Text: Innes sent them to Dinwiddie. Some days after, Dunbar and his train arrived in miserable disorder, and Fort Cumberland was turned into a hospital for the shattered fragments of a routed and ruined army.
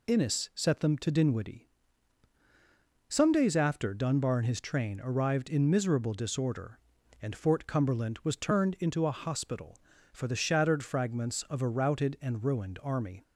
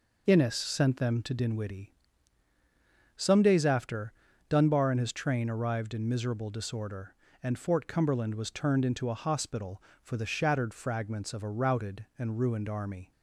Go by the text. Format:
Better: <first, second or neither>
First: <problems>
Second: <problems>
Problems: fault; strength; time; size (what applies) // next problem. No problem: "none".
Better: second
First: says "set" for "sent"; at 0.5 s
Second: none